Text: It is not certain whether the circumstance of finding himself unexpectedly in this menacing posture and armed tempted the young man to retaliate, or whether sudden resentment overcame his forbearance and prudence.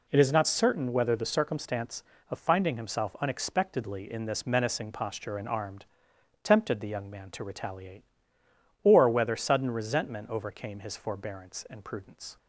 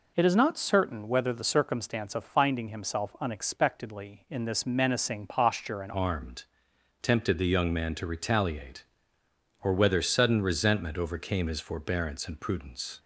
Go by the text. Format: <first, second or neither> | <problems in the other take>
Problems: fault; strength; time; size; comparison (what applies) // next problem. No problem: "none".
first | changes voice at "armed"; from 5.9 s on; 7.0 s long // pauses between "armed" and "tempted"; noticeable; at 6.4 s; 0.58 s long; noticeable in the first